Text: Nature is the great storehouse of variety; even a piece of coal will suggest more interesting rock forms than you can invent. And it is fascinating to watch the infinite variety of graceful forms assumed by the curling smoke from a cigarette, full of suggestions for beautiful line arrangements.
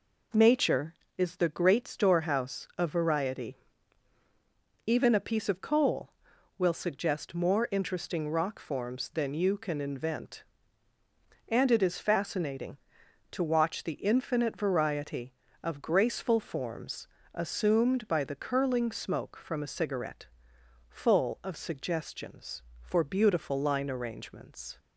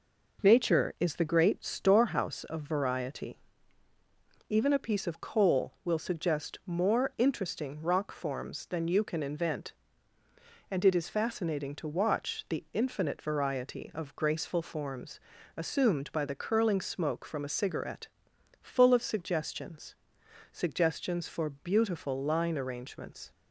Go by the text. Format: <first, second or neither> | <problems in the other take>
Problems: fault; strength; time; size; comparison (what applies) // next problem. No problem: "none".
first | pauses between "forms" and "assumed"; at 15.2 s; 0.38 s long; slight in the first // says "suggestions" twice; at 20.5 s